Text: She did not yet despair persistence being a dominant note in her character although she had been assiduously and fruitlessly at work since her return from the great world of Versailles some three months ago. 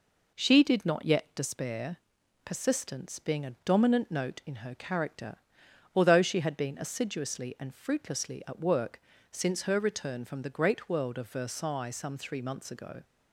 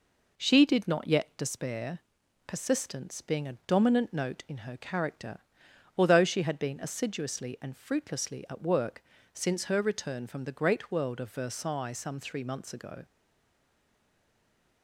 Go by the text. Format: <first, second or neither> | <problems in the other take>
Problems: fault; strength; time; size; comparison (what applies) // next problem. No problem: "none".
first | pauses between "despair" and "persistence"; noticeable; at 1.9 s; 0.48 s long; noticeable in the first // pauses between "character" and "although"; noticeable; at 5.3 s; 0.58 s long; noticeable in the first // pauses between "work" and "since"; slight; at 9.0 s; 0.28 s long; slight in the first // stays silent after the last word; noticeable; from 13.0 s on; 1.8 s long